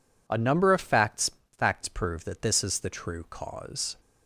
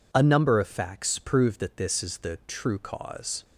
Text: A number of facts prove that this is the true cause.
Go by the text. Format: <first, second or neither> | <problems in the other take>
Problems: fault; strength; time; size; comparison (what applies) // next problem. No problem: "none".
second | says "facts" twice; at 1.5 s